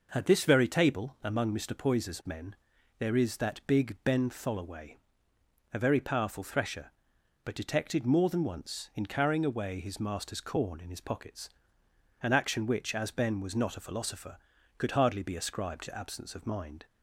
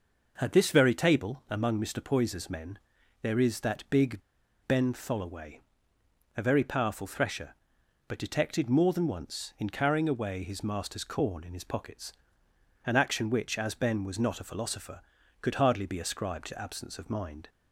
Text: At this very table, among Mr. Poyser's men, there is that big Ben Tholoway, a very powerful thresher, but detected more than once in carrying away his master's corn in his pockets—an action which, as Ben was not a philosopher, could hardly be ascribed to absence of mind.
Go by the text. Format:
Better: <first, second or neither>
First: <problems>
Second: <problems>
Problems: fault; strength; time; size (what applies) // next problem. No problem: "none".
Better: first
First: none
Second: pauses between "big" and "Ben"; noticeable; at 4.2 s; 0.46 s long